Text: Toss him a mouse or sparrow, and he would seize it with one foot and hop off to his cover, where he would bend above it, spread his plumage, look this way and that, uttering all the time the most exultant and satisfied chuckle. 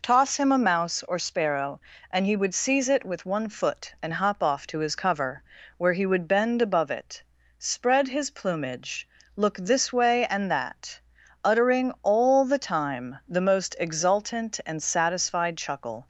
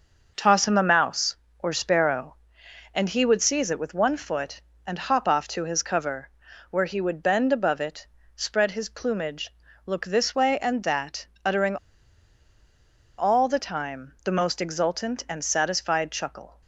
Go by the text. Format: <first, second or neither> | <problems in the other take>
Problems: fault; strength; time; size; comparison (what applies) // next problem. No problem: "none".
first | starts louder than the rest; noticeable; until 1.3 s; 6 dB // pauses between "uttering" and "all"; strong; at 11.7 s; 1.4 s long